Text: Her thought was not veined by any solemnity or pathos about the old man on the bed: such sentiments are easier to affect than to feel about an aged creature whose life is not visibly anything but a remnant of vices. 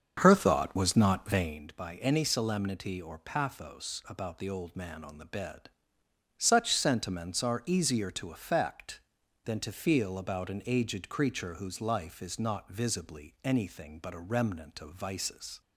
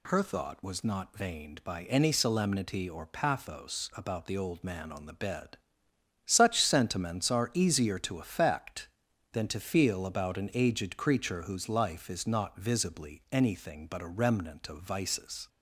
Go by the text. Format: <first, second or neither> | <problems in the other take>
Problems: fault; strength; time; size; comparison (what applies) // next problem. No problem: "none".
second | starts louder than the rest; until 1.7 s; 7 dB